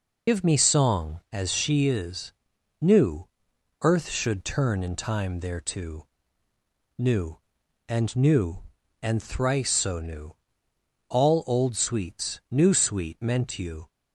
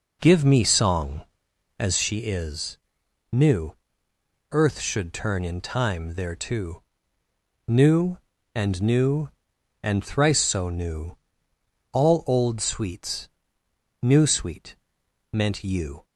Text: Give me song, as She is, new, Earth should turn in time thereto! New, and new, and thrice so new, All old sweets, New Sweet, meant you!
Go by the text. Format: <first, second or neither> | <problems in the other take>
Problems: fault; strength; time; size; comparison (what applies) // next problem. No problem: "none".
second | loses the start of "Give"; at 0.2 s; 80 ms